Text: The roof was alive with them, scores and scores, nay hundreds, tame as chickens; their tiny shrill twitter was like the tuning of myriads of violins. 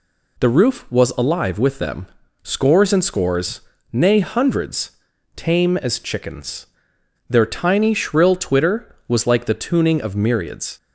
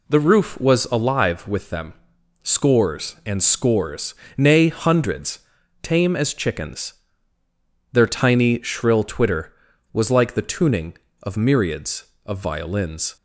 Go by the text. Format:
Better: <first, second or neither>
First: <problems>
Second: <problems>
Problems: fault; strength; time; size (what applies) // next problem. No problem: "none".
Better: second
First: stops before "of violins"; at 10.7 s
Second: none